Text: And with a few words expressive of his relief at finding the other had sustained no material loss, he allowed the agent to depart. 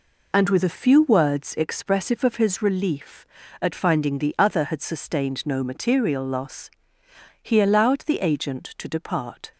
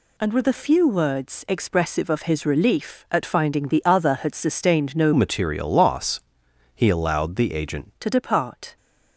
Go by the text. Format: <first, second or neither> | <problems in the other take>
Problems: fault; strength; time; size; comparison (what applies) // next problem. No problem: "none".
first | changes voice from "material" to "agent"; from 5.1 to 7.9 s; 2.8 s long